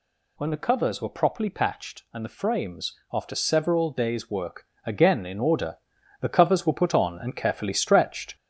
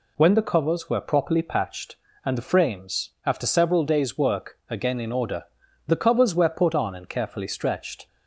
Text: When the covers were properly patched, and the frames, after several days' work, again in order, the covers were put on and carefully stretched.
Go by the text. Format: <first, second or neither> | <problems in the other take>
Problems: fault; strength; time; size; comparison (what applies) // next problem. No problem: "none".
second | gets louder; noticeable; throughout; 4 dB